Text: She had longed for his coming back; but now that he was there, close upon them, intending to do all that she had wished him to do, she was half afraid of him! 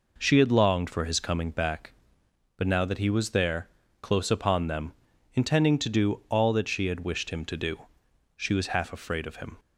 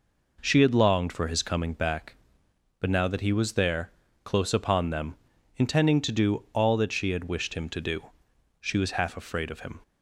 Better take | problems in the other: neither | none

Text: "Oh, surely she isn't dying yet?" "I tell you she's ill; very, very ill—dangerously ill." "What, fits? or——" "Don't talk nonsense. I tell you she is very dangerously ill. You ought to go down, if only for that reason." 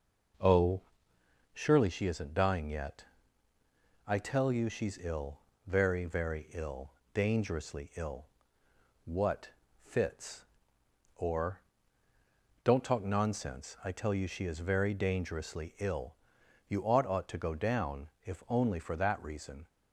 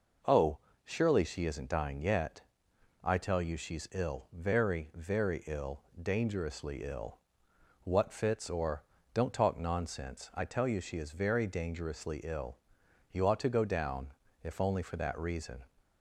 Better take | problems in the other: second | says "ought" twice; at 17.0 s

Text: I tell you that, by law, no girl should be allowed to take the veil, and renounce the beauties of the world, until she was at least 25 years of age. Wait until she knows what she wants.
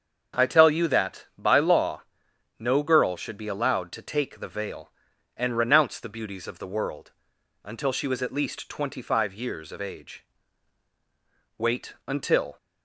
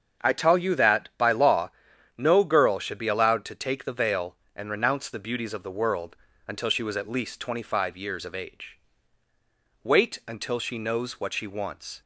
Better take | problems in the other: second | starts louder than the rest; until 1.4 s; 7 dB; strong in the second // stops before "she knows what she wants"; at 12.5 s

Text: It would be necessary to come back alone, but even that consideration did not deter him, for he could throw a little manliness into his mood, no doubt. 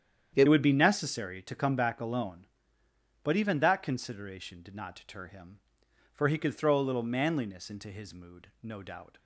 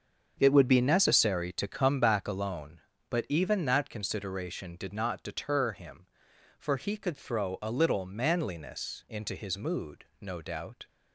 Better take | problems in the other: second | starts louder than the rest; strong; until 1.3 s; 9 dB; also in the second // changes voice at "would"; from 0.4 s on; 8.7 s long

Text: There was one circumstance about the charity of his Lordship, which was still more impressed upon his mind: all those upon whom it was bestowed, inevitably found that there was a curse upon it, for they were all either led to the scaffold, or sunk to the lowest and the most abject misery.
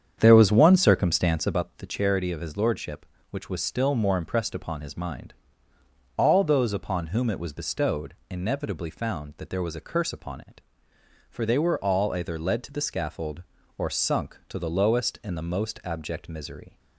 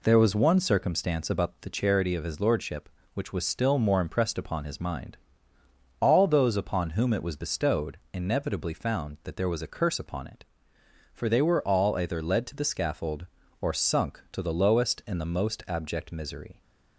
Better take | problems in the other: second | starts louder than the rest; strong; until 1.6 s; 8 dB

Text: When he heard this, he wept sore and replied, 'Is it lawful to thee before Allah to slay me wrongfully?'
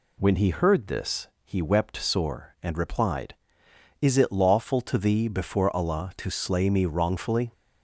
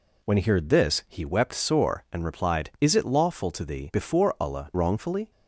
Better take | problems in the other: first | skips "to slay me"; at 4.7 s

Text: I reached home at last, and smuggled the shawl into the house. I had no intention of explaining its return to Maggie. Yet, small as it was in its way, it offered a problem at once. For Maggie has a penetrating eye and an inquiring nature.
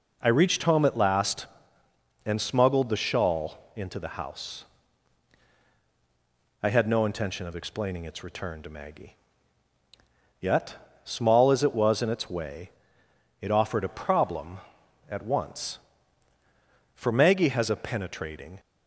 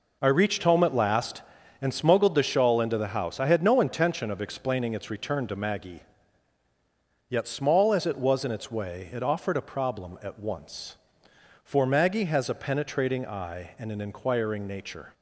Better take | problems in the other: second | stops before "eye and an inquiring nature"; at 18.5 s

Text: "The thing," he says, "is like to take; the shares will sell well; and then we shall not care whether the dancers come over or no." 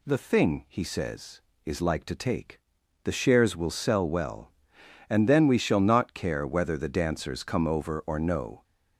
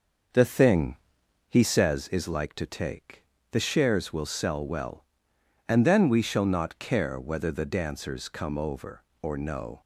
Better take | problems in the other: first | starts louder than the rest; until 2.1 s; 6.5 dB

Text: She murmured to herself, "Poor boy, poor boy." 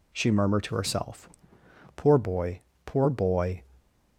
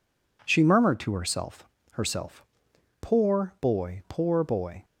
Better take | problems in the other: first | says "herself" twice; at 1.9 s

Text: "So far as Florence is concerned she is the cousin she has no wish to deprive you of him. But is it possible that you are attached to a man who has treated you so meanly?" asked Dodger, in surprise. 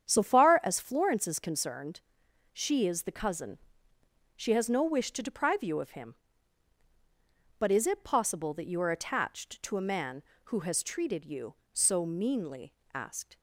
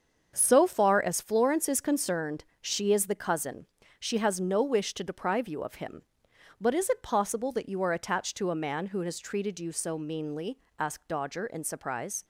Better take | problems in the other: second | starts louder than the rest; strong; until 1.1 s; 8.5 dB; also in the second // pauses between "concerned" and "she"; noticeable; at 2.0 s; 0.50 s long; slight in the second // pauses between "cousin" and "she"; noticeable; at 3.5 s; 0.78 s long; slight in the second // stops before "Dodger in surprise"; at 13.3 s

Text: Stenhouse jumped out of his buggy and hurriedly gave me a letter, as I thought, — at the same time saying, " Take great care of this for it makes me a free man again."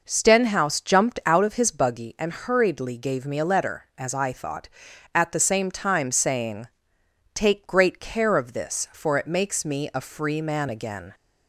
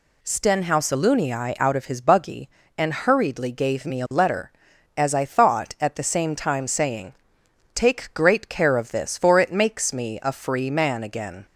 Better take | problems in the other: first | says "alunii" for "jumped"; at 0.9 s

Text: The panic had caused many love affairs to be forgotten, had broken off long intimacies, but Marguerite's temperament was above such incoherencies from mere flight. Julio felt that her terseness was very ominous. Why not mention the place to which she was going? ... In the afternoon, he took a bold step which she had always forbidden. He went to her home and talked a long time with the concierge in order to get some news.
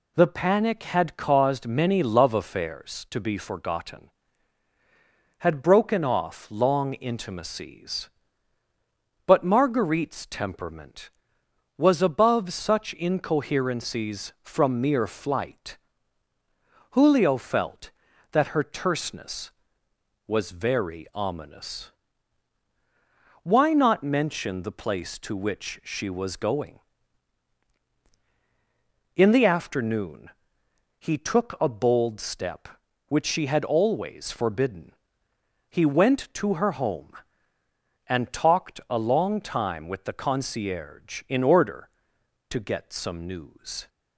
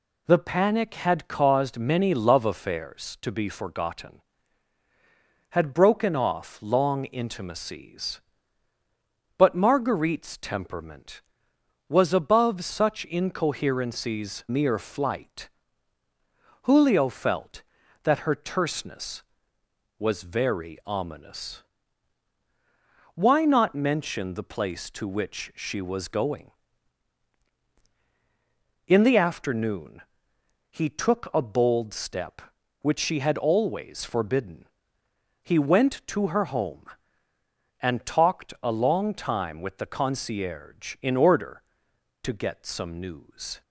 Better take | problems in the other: first | skips "from"; at 14.4 s

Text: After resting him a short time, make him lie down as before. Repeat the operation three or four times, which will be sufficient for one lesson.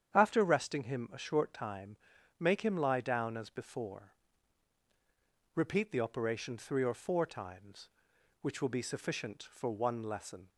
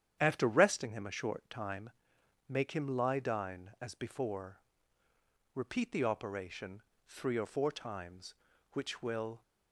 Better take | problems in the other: first | starts louder than the rest; strong; until 1.2 s; 9.5 dB; strong in the first // pauses between "operation" and "three"; slight; at 6.8 s; 0.24 s long // stops before "be sufficient for one lesson"; at 9.4 s

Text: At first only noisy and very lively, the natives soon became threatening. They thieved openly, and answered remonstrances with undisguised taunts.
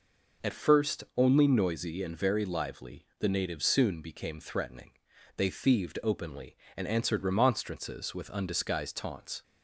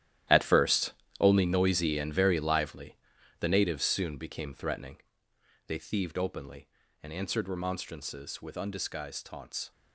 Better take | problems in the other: first | gets quieter; strong; throughout; 13 dB // pauses between "first" and "only"; slight; at 0.9 s; 0.26 s long

